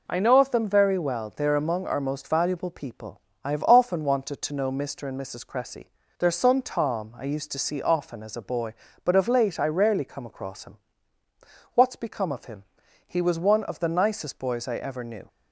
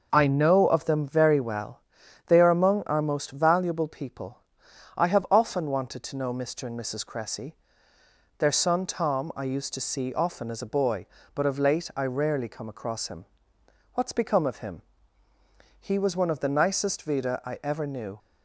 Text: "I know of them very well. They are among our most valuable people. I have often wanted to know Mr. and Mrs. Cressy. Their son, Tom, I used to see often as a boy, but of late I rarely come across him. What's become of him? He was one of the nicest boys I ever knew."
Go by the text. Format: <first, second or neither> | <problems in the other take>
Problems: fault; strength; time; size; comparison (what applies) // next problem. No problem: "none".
first | says "vida" for "boys"; at 17.0 s